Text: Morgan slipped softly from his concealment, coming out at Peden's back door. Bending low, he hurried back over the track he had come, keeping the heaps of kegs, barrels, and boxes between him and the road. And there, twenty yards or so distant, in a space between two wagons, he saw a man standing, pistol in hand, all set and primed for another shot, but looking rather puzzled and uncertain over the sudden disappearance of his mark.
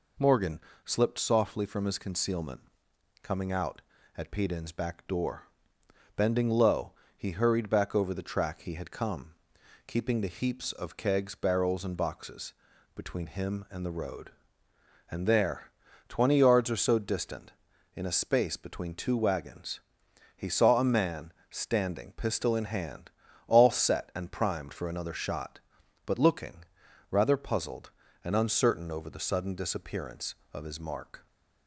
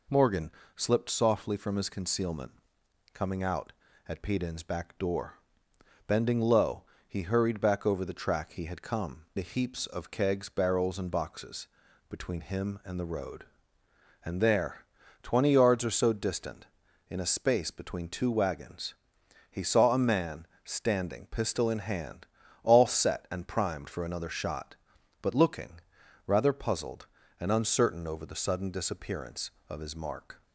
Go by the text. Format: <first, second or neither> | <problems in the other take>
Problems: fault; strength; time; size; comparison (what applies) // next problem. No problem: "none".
first | pauses between "Morgan" and "slipped"; slight; at 0.4 s; 0.26 s long; slight in the first // skips "keeping"; at 9.2 s // pauses between "boxes" and "between"; at 11.6 s; 0.44 s long; also in the first // pauses between "man" and "standing"; slight; at 20.4 s; 0.18 s long; slight in the first // pauses between "looking" and "rather"; noticeable; at 25.8 s; 0.46 s long; noticeable in the first